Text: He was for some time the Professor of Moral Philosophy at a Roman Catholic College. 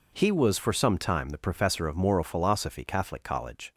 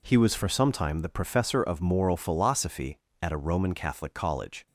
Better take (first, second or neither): second